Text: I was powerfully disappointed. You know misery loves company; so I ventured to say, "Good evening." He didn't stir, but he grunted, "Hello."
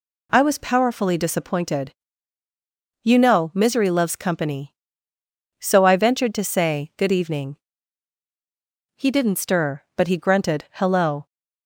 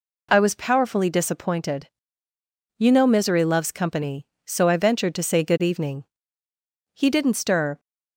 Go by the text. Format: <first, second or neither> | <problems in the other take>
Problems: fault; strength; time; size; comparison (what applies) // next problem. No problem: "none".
first | stops before "but he grunted Hello"; at 7.7 s